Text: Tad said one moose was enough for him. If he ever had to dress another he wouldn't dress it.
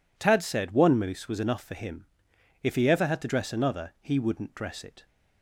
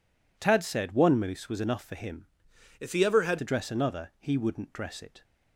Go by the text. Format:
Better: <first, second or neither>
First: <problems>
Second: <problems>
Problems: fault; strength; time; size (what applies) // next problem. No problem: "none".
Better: first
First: none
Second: changes voice from "If" to "had"; from 2.7 to 3.3 s; 0.6 s long